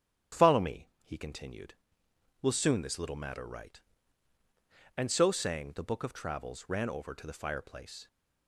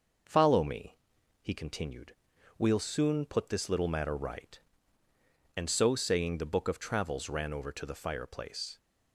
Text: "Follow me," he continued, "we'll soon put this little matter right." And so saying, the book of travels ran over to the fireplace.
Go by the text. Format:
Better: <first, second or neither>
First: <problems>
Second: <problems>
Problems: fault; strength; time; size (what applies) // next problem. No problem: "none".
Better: second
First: starts louder than the rest; strong; until 1.4 s; 10.5 dB // skips "put"; at 2.8 s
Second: none